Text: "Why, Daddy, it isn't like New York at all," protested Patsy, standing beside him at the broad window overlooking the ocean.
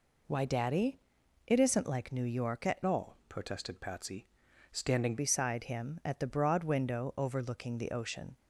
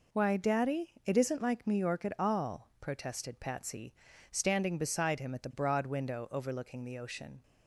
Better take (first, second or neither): second